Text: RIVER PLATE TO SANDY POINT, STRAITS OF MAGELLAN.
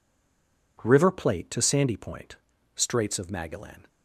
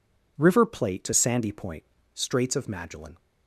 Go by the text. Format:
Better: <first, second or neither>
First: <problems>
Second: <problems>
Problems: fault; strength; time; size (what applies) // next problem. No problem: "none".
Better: second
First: stays silent before the first word; slight; until 0.7 s; 0.7 s long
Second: none